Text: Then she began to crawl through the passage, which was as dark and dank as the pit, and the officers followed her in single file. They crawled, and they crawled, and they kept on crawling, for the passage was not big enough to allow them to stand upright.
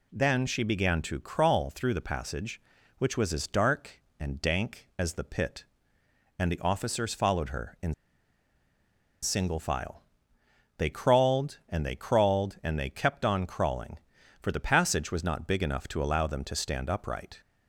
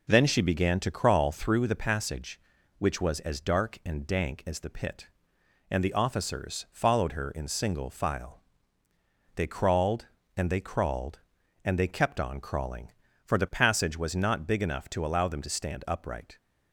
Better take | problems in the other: second | pauses between "in" and "single"; strong; at 7.9 s; 1.2 s long

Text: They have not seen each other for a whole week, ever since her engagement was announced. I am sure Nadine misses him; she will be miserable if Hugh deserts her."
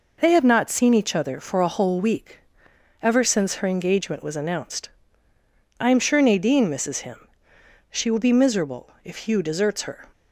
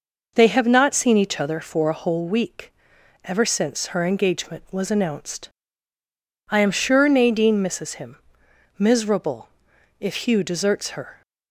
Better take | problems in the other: first | skips "she will be"; at 8.4 s // pauses between "miserable" and "if"; noticeable; at 9.4 s; 0.50 s long; slight in the first

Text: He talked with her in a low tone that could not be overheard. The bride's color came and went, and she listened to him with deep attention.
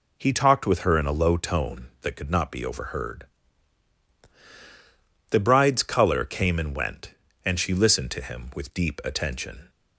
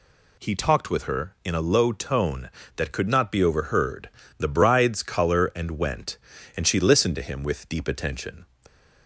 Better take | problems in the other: first | skips "came"; at 5.5 s

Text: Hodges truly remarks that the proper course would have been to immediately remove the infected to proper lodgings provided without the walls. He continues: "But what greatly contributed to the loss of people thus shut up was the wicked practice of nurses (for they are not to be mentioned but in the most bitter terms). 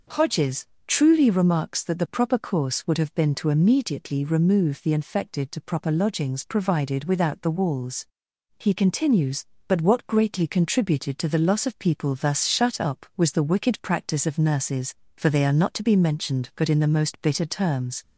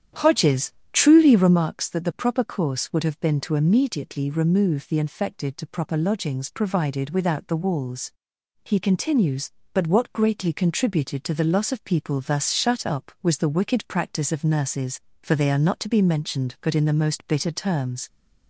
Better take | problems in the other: first | starts louder than the rest; strong; until 1.6 s; 9.5 dB // pauses between "Hodges" and "truly"; slight; at 0.7 s; 0.22 s long; slight in the first

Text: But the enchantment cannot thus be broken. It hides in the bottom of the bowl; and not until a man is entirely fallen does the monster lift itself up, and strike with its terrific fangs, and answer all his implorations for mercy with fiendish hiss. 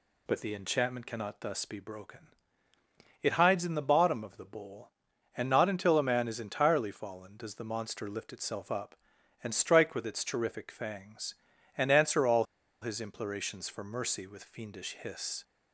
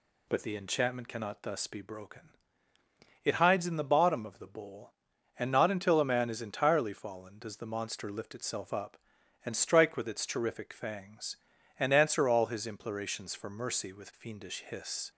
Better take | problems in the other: second | pauses between "all" and "his"; at 12.4 s; 0.38 s long

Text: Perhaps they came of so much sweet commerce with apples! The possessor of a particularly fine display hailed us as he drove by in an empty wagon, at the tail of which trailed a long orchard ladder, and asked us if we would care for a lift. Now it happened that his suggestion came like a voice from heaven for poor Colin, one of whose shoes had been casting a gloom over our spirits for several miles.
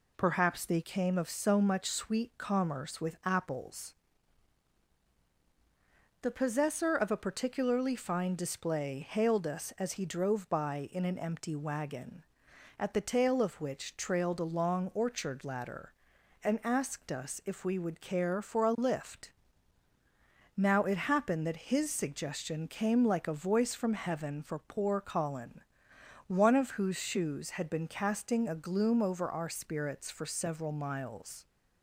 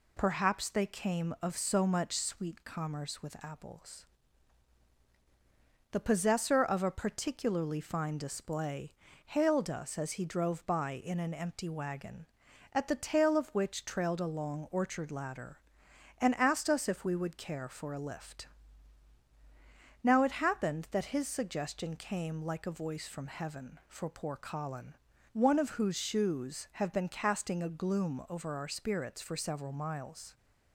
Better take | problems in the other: first | pauses between "display" and "hailed"; slight; at 8.9 s; 0.32 s long // says "have" for "had"; at 26.7 s

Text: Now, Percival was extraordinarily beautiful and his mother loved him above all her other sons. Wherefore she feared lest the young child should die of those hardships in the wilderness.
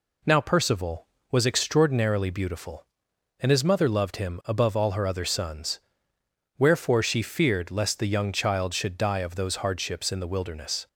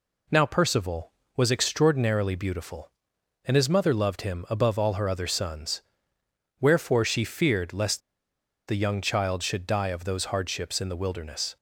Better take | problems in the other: first | pauses between "lest" and "the"; noticeable; at 8.0 s; 0.67 s long

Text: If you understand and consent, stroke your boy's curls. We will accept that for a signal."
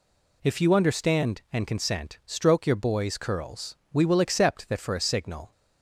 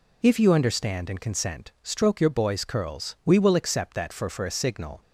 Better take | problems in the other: first | says "for" twice; at 4.3 s

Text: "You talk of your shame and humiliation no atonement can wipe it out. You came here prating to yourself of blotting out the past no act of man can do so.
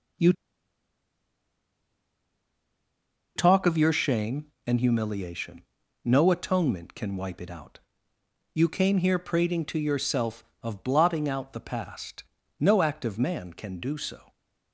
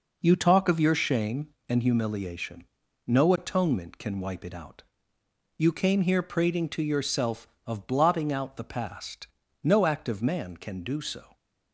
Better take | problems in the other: second | pauses between "You" and "talk"; strong; at 0.3 s; 3.0 s long // pauses between "humiliation" and "no"; at 5.6 s; 0.42 s long; also in the second // pauses between "past" and "no"; slight; at 12.2 s; 0.34 s long; slight in the second

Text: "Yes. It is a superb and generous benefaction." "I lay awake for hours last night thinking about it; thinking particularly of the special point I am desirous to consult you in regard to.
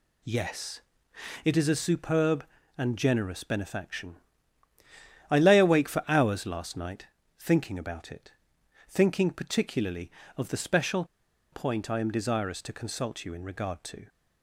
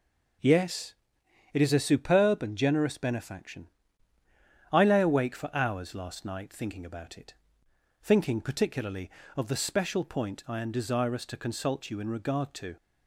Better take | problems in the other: second | pauses between "night" and "thinking"; slight; at 7.0 s; 0.34 s long // pauses between "special" and "point"; noticeable; at 11.0 s; 0.48 s long

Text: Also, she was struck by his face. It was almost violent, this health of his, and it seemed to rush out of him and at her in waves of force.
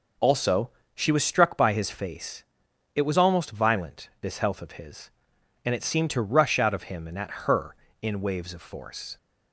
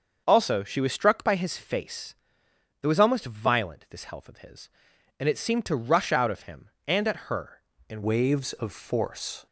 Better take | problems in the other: first | starts louder than the rest; until 1.2 s; 6.5 dB // changes voice at "waves"; from 8.0 s on; 1.4 s long

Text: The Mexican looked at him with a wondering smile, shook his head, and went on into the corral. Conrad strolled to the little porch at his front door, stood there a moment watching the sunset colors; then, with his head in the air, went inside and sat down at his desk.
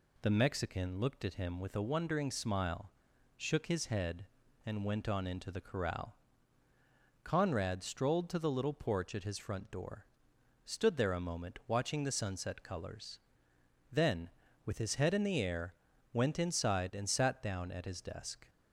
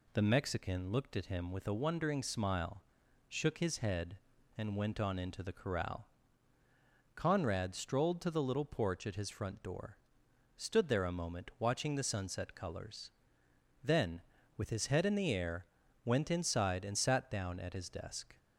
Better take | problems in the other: neither | none

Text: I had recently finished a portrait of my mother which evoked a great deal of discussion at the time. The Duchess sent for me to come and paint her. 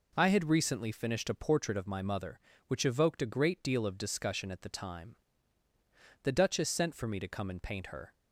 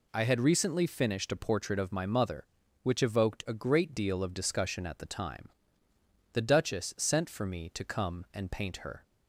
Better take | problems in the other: neither | none

